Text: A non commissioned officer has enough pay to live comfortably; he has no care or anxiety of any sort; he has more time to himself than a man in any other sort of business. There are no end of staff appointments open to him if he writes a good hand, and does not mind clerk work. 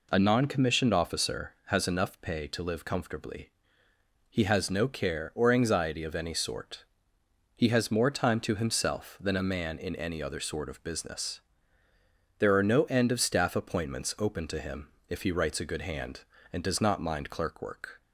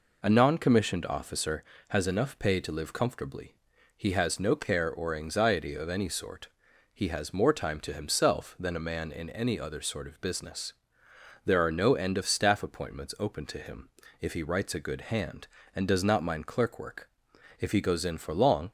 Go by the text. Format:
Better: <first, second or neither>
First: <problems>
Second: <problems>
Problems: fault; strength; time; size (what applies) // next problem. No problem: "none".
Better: first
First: pauses between "him" and "if"; slight; at 14.8 s; 0.22 s long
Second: pauses between "him" and "if"; slight; at 13.8 s; 0.30 s long // goes on to say "If he goes in for long"; noticeable; from 17.5 s on; 1.1 s long